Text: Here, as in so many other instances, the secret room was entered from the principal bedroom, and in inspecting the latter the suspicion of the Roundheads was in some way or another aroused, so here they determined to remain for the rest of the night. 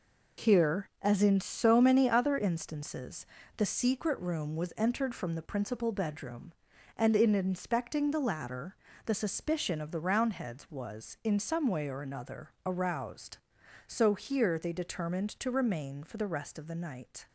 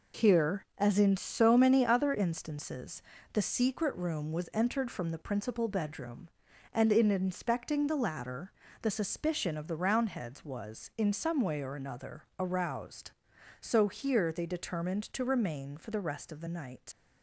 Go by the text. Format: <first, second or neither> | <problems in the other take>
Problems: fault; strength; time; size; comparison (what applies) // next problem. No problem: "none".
first | pauses between "latter" and "the"; slight; at 8.5 s; 0.28 s long; slight in the first // pauses between "another" and "aroused"; slight; at 12.2 s; 0.16 s long; slight in the first // leaves "night" unfinished; at 16.9 s; 80 ms